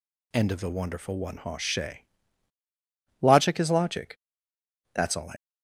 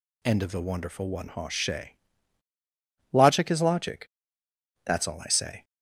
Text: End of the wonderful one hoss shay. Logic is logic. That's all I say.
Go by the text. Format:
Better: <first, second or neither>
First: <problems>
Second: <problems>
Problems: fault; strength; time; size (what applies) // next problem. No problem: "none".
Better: second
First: stops before "say"; at 5.3 s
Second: none